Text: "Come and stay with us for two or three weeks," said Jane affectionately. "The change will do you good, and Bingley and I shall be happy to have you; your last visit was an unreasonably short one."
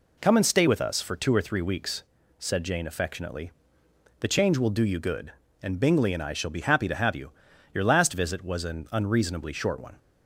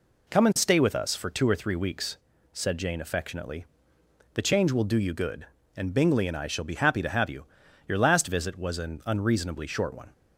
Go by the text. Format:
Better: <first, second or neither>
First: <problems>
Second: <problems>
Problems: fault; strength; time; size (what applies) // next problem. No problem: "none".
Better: neither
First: none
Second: none